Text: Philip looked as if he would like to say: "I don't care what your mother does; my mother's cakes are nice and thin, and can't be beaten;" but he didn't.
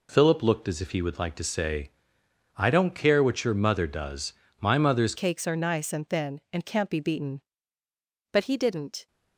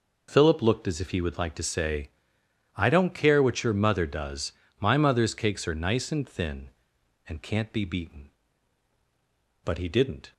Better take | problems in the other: second | changes voice at "cakes"; from 5.1 s on; 3.9 s long

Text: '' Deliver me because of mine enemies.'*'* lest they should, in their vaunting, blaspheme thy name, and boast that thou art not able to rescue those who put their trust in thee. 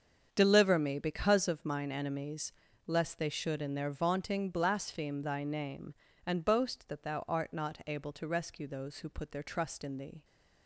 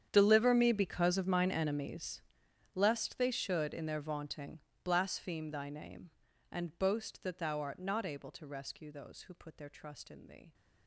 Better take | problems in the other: first | gets quieter; strong; throughout; 20 dB // starts louder than the rest; strong; until 1.1 s; 9 dB; strong in the first

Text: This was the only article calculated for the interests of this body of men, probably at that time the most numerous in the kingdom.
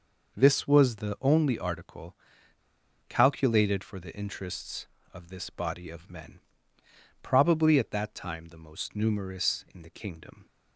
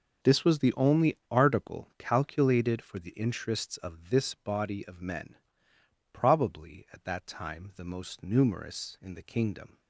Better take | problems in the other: second | pauses between "article" and "calculated"; noticeable; at 2.1 s; 0.92 s long

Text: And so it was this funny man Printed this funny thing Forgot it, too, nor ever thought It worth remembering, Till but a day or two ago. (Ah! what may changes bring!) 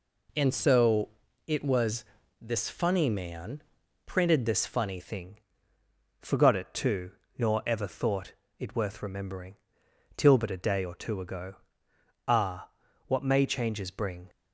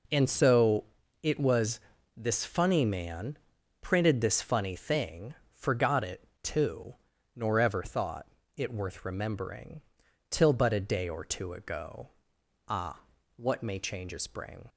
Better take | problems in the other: second | pauses between "so" and "it"; at 1.0 s; 0.38 s long; also in the second // pauses between "was" and "this"; slight; at 2.0 s; 0.36 s long; slight in the second // pauses between "man" and "Printed"; at 3.6 s; 0.44 s long; also in the second // changes voice at "thing"; from 4.9 s on; 9.3 s long // pauses between "thing" and "Forgot"; noticeable; at 5.3 s; 0.82 s long; slight in the second // pauses between "thought" and "It"; slight; at 8.3 s; 0.24 s long; slight in the second

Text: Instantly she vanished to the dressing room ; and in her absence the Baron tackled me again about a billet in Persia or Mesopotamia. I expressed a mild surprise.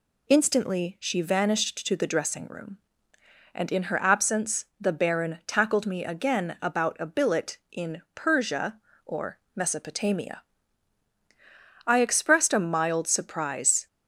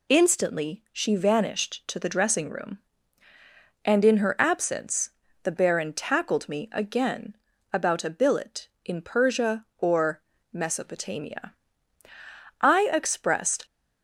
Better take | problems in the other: first | pauses between "absence" and "the"; slight; at 5.0 s; 0.32 s long; slight in the first // pauses between "again" and "about"; at 7.3 s; 0.38 s long // pauses between "or" and "Mesopotamia"; slight; at 10.2 s; 0.32 s long; slight in the first // stops before "a mild surprise"; at 13.6 s

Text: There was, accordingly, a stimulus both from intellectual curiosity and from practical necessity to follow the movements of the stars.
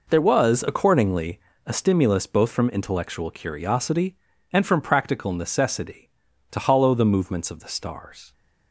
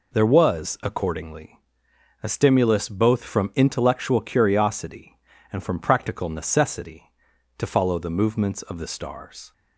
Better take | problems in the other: second | says "hollow" for "follow"; at 6.6 s

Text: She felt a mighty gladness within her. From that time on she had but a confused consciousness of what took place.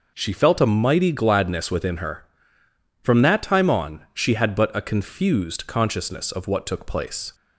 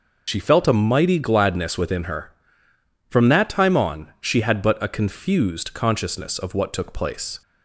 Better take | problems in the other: first | loses the start of "She"; at 0.2 s; 65 ms

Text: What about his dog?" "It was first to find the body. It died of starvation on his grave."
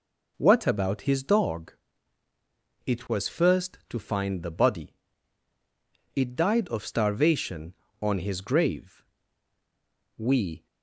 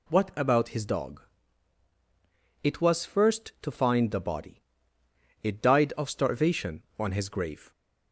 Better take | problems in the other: second | goes on to say "We"; slight; from 10.1 s on; 0.48 s long

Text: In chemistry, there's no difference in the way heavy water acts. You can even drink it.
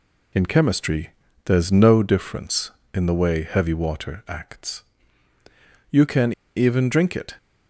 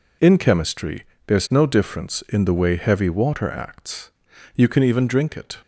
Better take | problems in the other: second | pauses between "can" and "even"; slight; at 6.3 s; 0.24 s long

